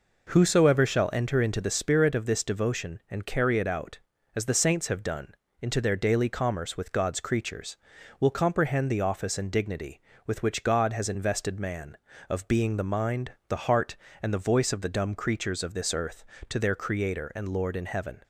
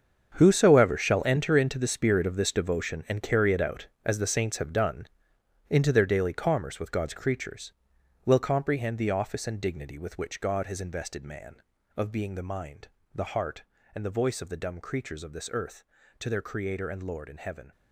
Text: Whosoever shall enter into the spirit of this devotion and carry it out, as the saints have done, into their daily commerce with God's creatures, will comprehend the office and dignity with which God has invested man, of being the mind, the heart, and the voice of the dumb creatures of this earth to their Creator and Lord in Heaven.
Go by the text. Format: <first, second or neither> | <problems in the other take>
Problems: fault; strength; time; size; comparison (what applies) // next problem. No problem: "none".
first | gets quieter; strong; throughout; 13 dB